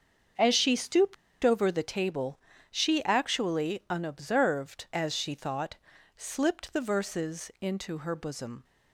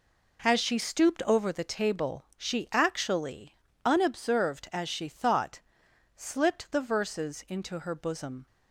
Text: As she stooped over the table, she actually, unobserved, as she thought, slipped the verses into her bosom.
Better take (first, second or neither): second